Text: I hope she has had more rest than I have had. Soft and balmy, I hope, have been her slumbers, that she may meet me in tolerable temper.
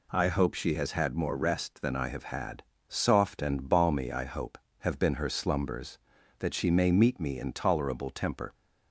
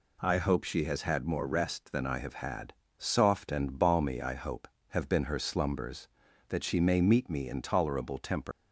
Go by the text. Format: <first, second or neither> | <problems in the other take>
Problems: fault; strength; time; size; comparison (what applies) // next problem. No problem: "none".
first | leaves "temper" unfinished; at 8.5 s; 95 ms